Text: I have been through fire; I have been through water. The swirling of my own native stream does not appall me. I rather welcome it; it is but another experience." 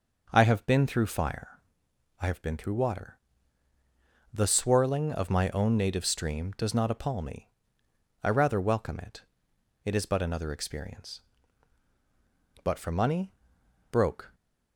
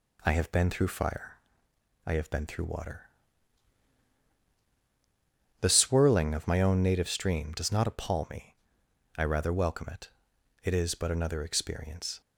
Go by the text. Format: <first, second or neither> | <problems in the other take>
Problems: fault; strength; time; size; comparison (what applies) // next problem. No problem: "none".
second | goes on to say "But for money broke"; strong; from 12.6 s on; 1.7 s long